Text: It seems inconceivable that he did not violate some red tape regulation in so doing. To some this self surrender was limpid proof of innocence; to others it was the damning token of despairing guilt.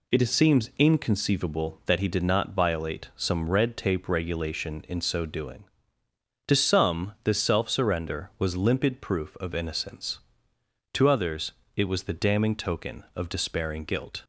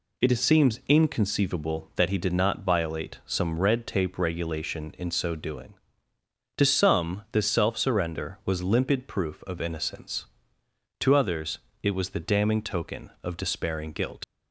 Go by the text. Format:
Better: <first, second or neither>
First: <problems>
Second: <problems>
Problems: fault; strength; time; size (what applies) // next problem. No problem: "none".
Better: first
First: pauses between "others" and "it"; slight; at 11.5 s; 0.24 s long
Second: pauses between "others" and "it"; slight; at 11.5 s; 0.24 s long // leaves "guilt" unfinished; at 14.2 s; 75 ms